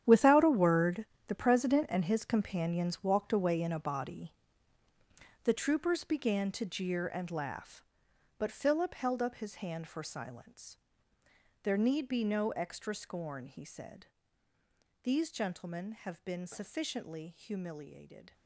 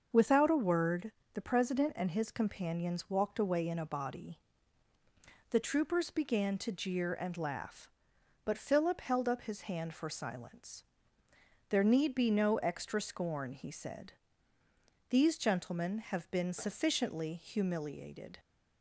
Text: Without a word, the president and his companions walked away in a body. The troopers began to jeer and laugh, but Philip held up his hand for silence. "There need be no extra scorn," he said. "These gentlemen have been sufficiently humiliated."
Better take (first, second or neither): second